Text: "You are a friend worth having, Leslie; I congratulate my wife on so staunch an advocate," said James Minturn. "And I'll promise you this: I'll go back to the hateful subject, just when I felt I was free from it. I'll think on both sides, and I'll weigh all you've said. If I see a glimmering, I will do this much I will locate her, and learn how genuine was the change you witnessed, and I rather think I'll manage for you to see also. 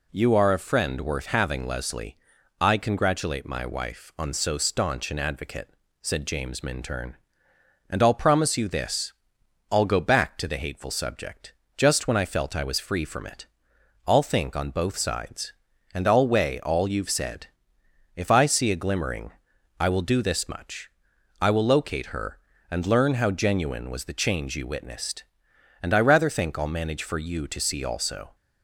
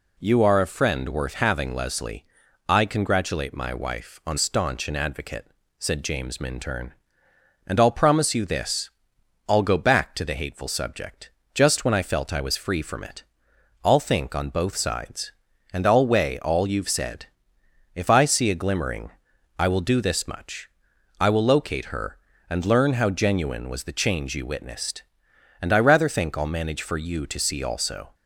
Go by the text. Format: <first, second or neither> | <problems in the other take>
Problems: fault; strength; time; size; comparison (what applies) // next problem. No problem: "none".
first | skips "so"; at 4.3 s // pauses between "much" and "I"; noticeable; at 20.6 s; 0.52 s long; noticeable in the first